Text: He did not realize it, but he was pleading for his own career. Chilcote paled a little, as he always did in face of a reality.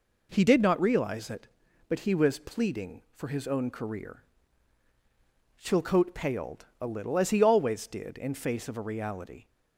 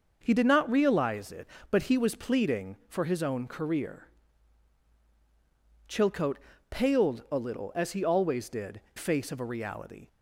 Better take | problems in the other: first | pauses between "Chilcote" and "paled"; slight; at 6.3 s; 0.32 s long // skips "in"; at 8.8 s

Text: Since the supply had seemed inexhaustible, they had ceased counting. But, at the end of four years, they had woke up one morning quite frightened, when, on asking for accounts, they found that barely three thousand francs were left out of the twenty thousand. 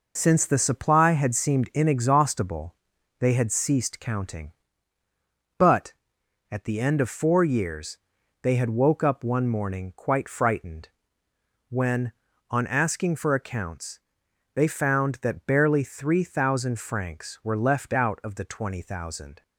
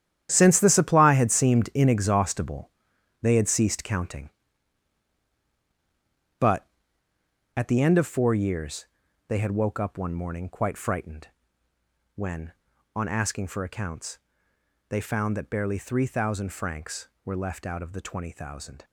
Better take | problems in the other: first | gets quieter; strong; throughout; 12.5 dB

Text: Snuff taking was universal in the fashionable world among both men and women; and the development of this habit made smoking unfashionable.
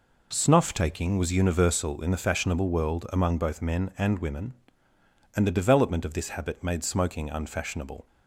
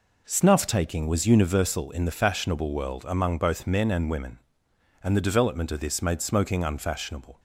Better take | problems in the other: first | skips "habit"; at 6.0 s

